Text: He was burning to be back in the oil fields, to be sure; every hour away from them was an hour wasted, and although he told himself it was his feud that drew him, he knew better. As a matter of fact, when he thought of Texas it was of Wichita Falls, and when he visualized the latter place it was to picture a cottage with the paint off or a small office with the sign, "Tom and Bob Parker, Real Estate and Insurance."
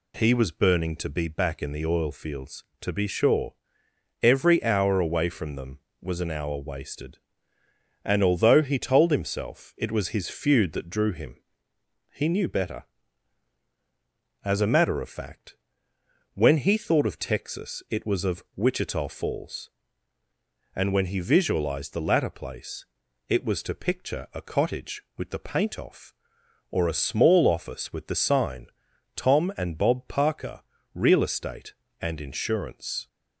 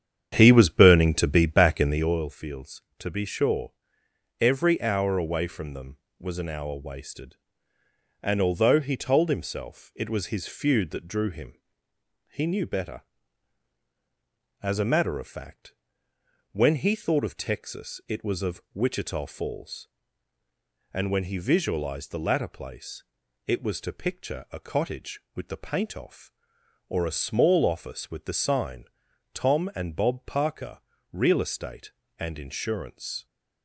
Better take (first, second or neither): first